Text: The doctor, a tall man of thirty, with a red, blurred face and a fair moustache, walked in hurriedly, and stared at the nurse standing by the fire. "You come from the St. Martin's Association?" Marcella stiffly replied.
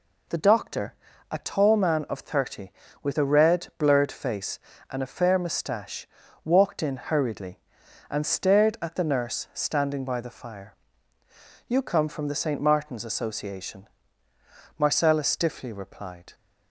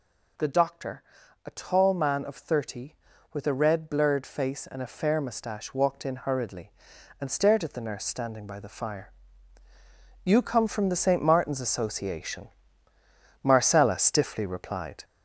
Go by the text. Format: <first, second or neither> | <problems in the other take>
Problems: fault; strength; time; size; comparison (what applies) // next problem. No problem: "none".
first | gets louder; noticeable; throughout; 5.5 dB